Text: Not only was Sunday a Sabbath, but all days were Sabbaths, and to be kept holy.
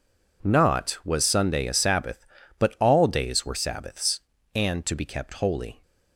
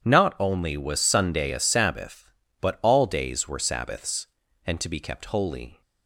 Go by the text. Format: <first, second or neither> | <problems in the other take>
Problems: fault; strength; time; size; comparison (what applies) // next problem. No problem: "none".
second | skips "only"; at 1.0 s